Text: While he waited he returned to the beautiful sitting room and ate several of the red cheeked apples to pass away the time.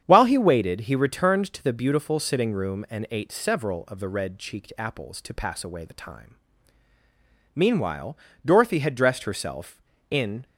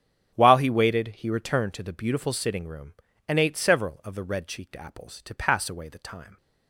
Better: second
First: starts louder than the rest; strong; until 1.0 s; 8.5 dB // goes on to say "Meanwhile Dorothy had dressed herself in"; strong; from 7.5 s on; 2.9 s long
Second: starts louder than the rest; strong; until 1.3 s; 9.5 dB

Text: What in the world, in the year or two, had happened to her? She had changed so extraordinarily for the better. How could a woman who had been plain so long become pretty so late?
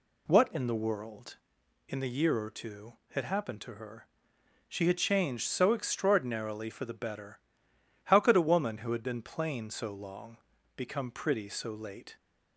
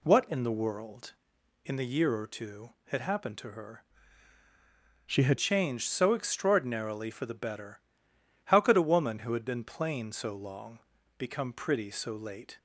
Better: first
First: pauses between "long" and "become"; at 10.3 s; 0.38 s long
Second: changes voice from "She" to "had"; from 5.0 to 5.3 s; 0.3 s long // pauses between "long" and "become"; at 10.7 s; 0.38 s long

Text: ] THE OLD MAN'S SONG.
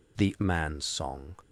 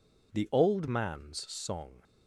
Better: second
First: skips "OLD"; at 0.3 s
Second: none

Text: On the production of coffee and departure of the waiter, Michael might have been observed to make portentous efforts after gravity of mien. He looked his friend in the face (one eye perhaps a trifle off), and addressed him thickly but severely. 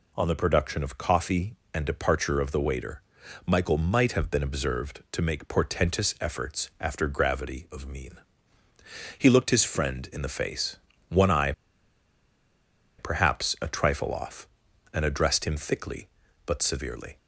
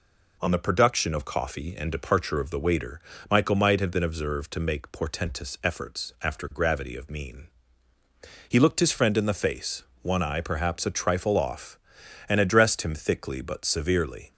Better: second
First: pauses between "eye" and "perhaps"; strong; at 11.5 s; 1.4 s long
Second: none

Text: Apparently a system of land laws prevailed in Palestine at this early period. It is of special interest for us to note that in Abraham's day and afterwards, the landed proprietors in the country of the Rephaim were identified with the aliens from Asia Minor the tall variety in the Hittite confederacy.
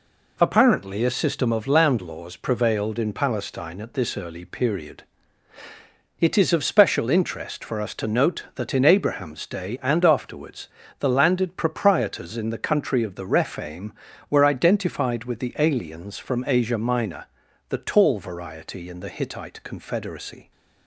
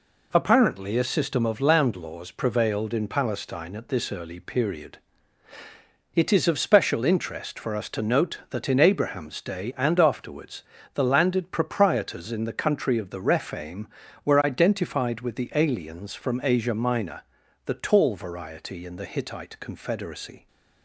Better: neither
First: pauses between "Minor" and "the"; at 17.2 s; 0.44 s long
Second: pauses between "Minor" and "the"; at 17.2 s; 0.44 s long

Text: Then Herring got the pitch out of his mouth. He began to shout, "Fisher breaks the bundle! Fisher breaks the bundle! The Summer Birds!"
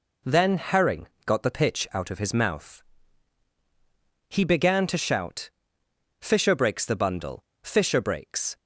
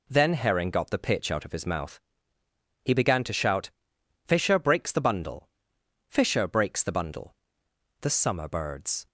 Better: second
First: pauses between "Herring" and "got"; slight; at 1.0 s; 0.20 s long // stops before "the bundle The Summer Birds"; at 8.5 s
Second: none

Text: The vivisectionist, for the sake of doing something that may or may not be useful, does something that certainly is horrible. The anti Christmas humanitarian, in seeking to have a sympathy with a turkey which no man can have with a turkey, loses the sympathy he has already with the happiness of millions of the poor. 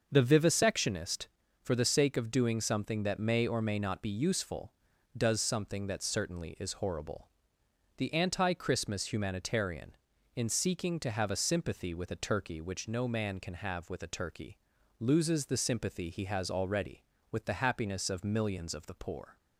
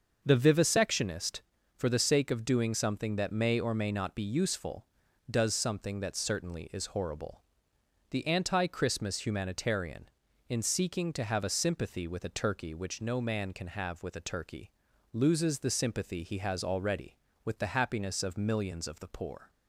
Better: neither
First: starts louder than the rest; noticeable; until 1.1 s; 6 dB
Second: starts louder than the rest; until 1.2 s; 6 dB

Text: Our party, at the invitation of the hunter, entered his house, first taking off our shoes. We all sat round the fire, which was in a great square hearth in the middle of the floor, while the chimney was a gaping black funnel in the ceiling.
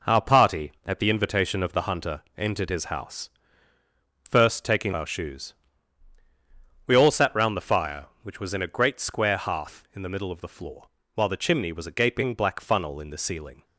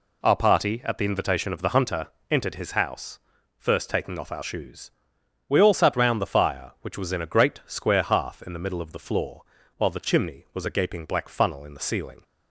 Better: second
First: skips "off"; at 4.9 s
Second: none

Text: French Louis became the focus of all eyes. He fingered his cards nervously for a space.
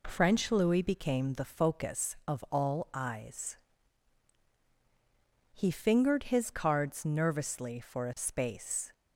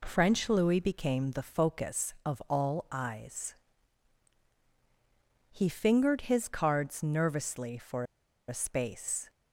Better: first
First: none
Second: pauses between "for" and "a"; at 8.0 s; 0.44 s long

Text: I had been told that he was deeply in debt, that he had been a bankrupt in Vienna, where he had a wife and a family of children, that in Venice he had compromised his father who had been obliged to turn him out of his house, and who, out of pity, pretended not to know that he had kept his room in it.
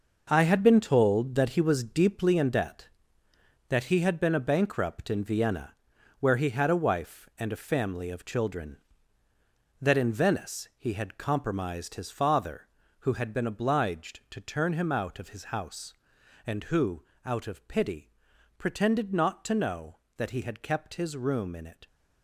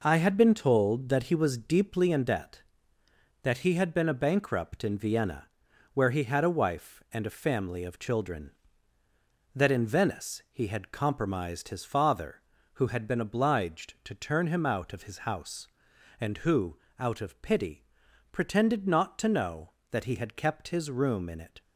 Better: second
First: gets quieter; strong; throughout; 9.5 dB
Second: none

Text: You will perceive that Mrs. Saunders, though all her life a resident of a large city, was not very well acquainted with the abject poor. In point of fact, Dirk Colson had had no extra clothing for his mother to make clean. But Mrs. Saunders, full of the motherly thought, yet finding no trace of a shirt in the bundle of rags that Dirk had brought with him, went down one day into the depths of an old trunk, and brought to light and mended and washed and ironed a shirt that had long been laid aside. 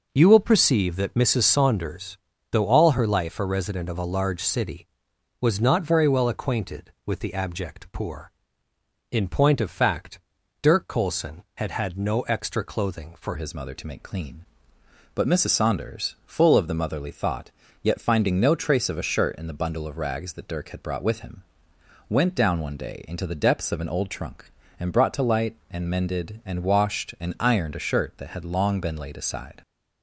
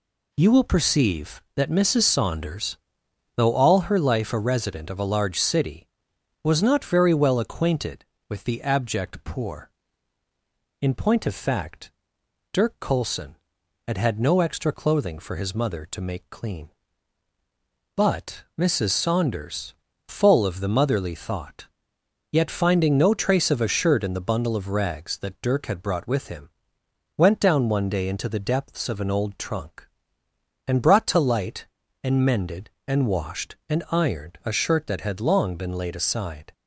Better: second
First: changes voice at "his"; from 13.3 s on; 16.3 s long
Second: none

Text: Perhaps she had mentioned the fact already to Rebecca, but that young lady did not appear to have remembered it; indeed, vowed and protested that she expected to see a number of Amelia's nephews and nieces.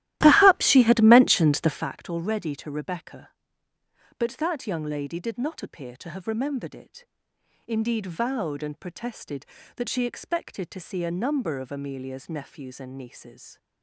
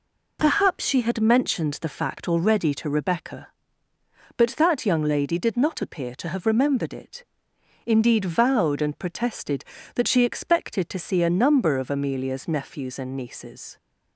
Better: second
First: starts louder than the rest; strong; until 1.9 s; 15 dB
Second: none

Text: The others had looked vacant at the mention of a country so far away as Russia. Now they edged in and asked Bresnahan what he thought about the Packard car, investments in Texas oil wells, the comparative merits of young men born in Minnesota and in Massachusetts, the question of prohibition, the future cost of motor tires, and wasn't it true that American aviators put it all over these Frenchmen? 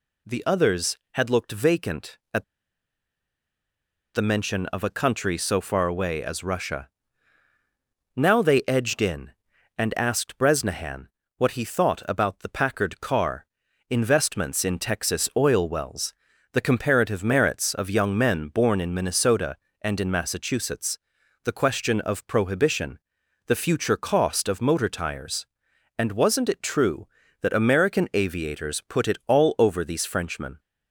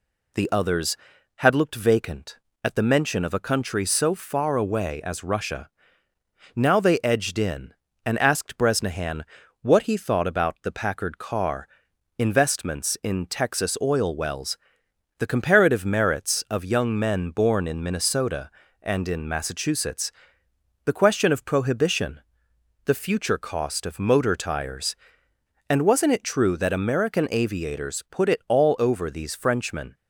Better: second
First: pauses between "at" and "the"; strong; at 2.4 s; 1.7 s long // pauses between "Bresnahan" and "what"; slight; at 11.0 s; 0.30 s long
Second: pauses between "Bresnahan" and "what"; slight; at 9.2 s; 0.36 s long

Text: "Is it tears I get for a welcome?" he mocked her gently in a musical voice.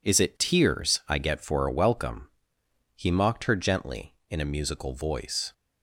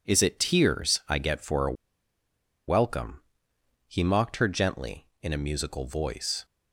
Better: first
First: none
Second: pauses between "a" and "welcome"; noticeable; at 1.7 s; 0.95 s long

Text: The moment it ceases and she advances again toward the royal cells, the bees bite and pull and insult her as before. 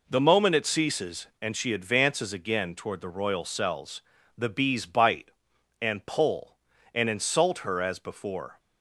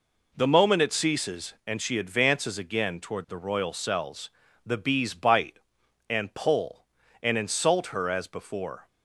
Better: neither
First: none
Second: none

